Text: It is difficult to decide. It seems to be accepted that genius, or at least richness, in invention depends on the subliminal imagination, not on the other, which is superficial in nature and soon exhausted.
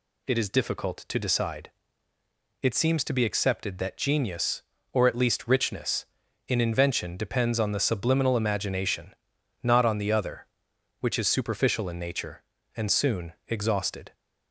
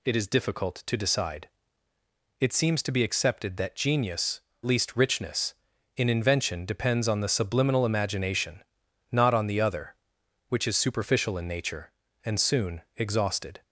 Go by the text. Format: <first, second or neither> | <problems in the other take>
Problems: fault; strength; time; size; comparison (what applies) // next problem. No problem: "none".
first | skips "or at"; at 4.5 s // pauses between "soon" and "exhausted"; slight; at 12.8 s; 0.16 s long; slight in the first